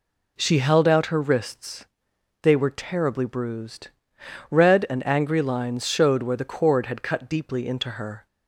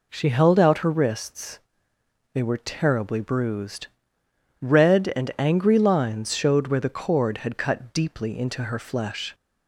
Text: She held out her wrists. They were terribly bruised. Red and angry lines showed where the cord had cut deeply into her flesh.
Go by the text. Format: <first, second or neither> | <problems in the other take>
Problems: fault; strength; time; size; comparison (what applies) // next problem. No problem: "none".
second | stops before "flesh"; at 8.2 s